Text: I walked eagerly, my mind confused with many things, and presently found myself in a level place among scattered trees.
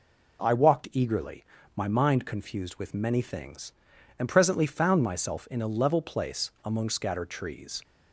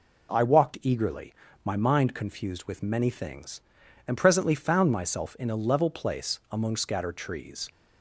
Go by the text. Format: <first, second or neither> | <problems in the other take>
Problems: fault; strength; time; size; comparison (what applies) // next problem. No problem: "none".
neither | none